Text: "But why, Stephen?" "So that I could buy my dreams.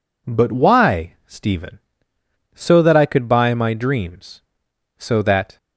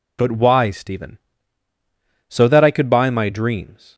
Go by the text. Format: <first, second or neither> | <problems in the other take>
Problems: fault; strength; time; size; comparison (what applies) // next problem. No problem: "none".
second | goes on to say "So that"; from 4.9 s on; 0.60 s long